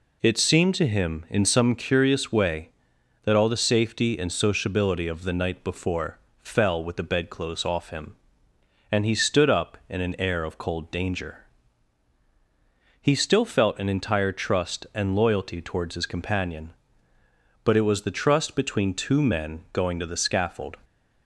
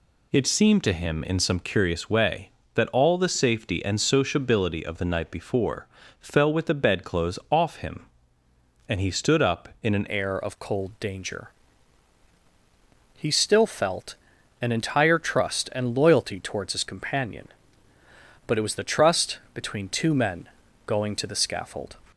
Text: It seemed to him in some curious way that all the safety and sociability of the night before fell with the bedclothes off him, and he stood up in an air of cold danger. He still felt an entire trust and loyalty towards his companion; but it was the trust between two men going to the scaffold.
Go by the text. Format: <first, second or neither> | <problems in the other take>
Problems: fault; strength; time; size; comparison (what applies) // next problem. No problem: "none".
first | pauses between "before" and "fell"; slight; at 5.8 s; 0.32 s long; slight in the first // changes voice at "air"; from 10.0 s on; 11.9 s long // pauses between "felt" and "an"; noticeable; at 14.1 s; 0.46 s long // pauses between "men" and "going"; at 20.4 s; 0.40 s long